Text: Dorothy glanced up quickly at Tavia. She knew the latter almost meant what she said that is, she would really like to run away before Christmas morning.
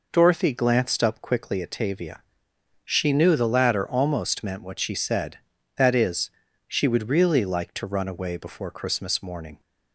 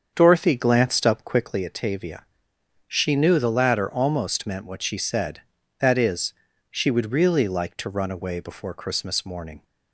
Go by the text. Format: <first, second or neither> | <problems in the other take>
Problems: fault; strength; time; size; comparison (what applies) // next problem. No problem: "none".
first | starts louder than the rest; until 1.6 s; 7 dB